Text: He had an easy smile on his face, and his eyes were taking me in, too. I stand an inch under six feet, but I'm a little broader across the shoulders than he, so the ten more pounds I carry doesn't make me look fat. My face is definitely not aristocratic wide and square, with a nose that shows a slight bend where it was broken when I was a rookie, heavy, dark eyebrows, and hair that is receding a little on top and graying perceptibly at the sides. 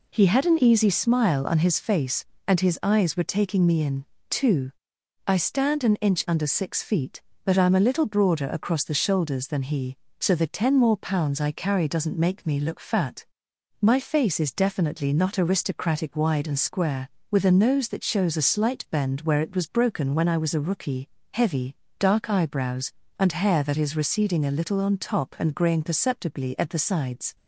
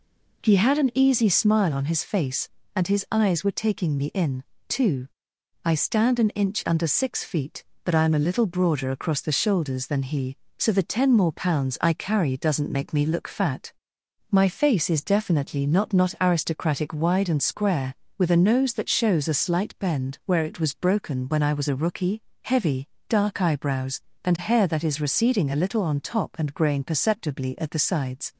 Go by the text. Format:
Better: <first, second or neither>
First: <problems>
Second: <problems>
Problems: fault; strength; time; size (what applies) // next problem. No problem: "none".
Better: first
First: none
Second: says "not" twice; at 15.9 s